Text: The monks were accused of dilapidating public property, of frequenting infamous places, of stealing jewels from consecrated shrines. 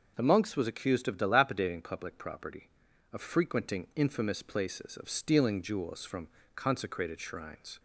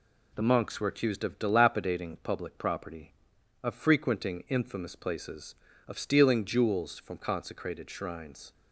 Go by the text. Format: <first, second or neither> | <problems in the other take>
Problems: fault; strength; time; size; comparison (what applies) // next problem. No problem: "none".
second | says "was" for "were"; at 0.5 s // pauses between "from" and "consecrated"; slight; at 6.2 s; 0.26 s long